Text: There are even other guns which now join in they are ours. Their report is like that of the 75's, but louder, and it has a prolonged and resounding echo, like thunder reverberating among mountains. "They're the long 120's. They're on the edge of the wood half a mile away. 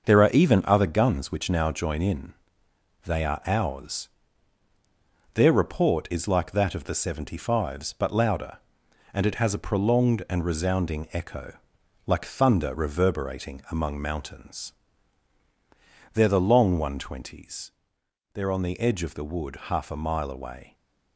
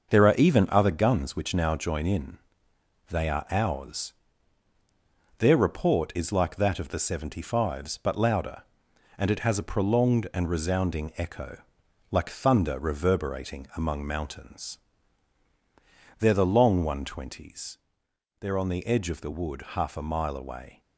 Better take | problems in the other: neither | starts louder than the rest; the same in both // pauses between "in" and "they"; noticeable; the same in both

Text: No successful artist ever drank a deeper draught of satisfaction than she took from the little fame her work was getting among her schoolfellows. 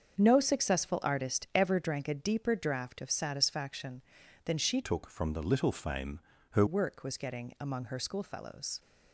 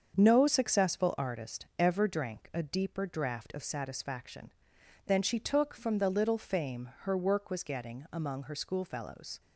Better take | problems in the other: second | starts louder than the rest; until 1.2 s; 7 dB; also in the second // changes voice from "took" to "her"; from 4.8 to 6.6 s; 1.8 s long // pauses between "fame" and "her"; slight; at 6.2 s; 0.30 s long

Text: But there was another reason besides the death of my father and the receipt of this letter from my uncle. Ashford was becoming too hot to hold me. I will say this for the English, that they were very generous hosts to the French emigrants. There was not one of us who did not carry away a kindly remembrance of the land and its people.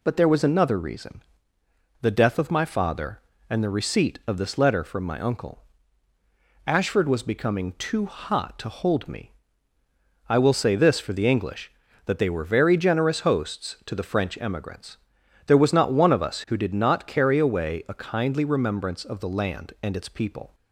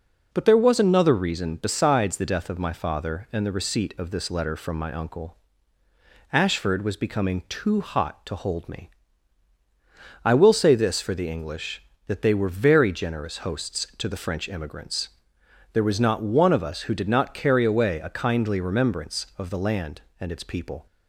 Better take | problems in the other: second | skips "besides"; at 1.6 s

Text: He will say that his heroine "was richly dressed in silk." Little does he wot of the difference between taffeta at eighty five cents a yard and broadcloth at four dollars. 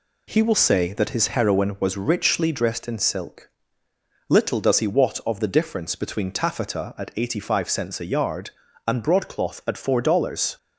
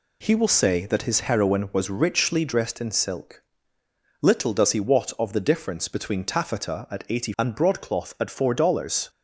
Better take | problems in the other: first | skips "five cents a yard"; at 7.3 s

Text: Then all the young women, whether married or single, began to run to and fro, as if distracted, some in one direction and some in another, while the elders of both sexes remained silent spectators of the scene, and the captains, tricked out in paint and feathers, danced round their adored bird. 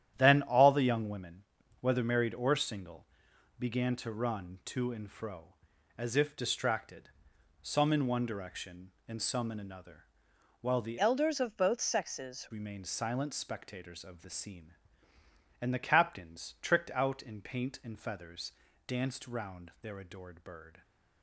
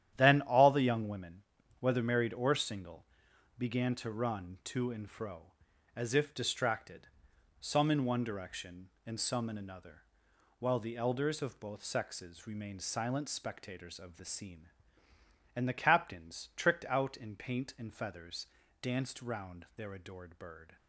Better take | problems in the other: second | starts louder than the rest; strong; until 1.1 s; 10.5 dB; strong in the second // changes voice from "elders" to "sexes"; from 10.9 to 12.4 s; 1.5 s long

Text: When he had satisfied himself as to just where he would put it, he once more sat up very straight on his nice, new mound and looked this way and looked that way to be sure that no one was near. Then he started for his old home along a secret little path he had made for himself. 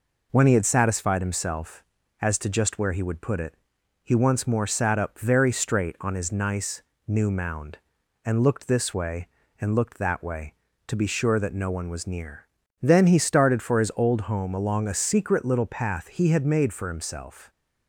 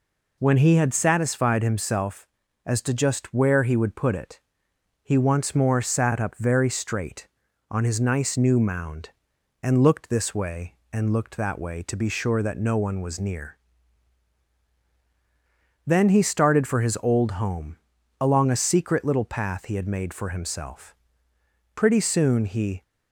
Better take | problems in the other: first | pauses between "home" and "along"; at 17.7 s; 0.44 s long // goes on to say "Pretty soon he"; noticeable; from 21.7 s on; 1.0 s long

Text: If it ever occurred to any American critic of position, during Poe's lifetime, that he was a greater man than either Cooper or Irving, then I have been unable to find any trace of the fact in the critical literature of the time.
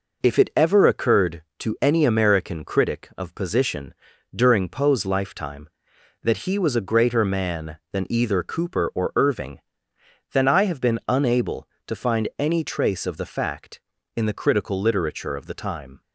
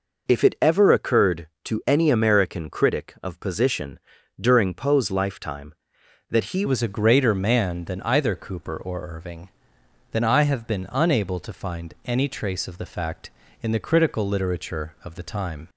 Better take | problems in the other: first | changes voice at "was"; from 6.6 s on; 9.0 s long

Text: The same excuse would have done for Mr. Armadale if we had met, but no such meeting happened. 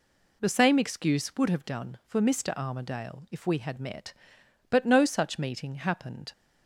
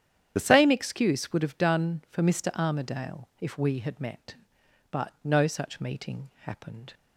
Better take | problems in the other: first | loses the start of "The"; at 0.3 s; 30 ms // starts louder than the rest; strong; until 1.3 s; 9.5 dB

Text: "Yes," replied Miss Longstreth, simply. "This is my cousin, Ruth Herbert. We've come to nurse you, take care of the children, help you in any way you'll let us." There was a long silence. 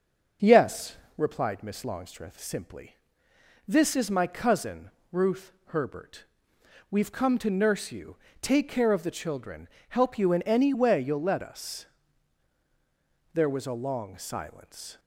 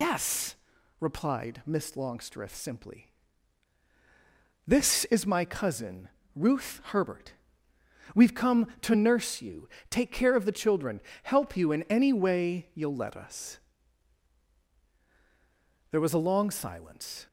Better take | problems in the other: first | loses the start of "Yes"; at 0.0 s; 85 ms

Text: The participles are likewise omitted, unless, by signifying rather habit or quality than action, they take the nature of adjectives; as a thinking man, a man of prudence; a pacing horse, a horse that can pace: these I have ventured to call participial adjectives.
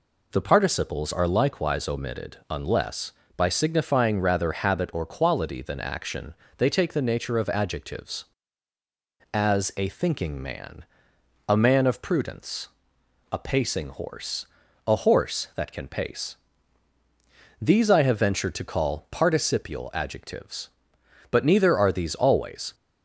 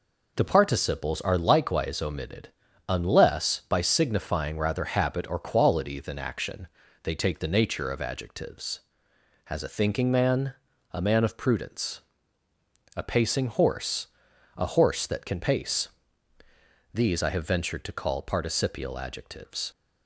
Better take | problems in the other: second | goes on to say "But neither are these always"; from 21.3 s on; 1.4 s long

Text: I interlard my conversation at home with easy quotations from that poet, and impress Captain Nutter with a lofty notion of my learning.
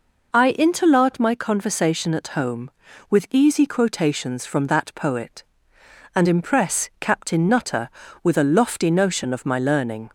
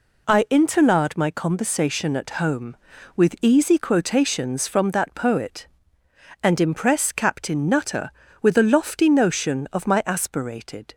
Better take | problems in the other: first | says "aspirated" for "learning"; at 10.0 s

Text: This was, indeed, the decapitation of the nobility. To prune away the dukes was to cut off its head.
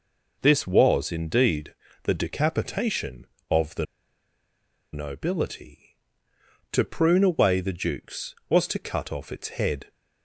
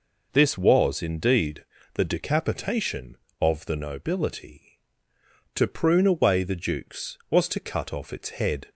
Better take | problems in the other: second | pauses between "the" and "nobility"; at 3.8 s; 1.0 s long

